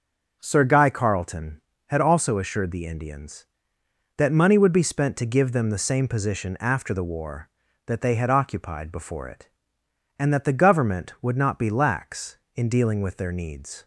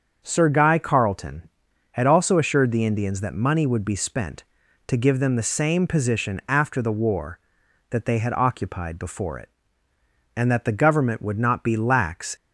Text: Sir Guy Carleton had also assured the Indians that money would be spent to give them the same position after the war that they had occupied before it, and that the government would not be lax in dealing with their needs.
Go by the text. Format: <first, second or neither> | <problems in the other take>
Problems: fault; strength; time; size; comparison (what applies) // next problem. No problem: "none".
first | starts louder than the rest; until 1.2 s; 6.5 dB // stops before "in dealing with their needs"; at 12.3 s